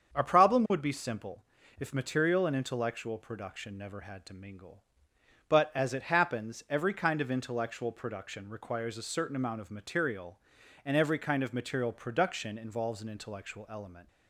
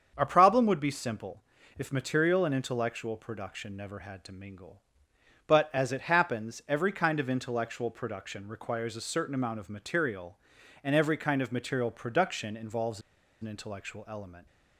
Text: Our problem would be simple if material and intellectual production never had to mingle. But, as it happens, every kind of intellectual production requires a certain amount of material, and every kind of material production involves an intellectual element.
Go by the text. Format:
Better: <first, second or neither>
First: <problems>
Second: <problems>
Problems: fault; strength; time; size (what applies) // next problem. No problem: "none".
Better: first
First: starts louder than the rest; strong; until 1.1 s; 7.5 dB // pauses between "simple" and "if"; slight; at 1.4 s; 0.34 s long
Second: starts louder than the rest; strong; until 1.1 s; 7.5 dB // pauses between "simple" and "if"; slight; at 1.4 s; 0.34 s long // pauses between "involves" and "an"; at 12.9 s; 0.41 s long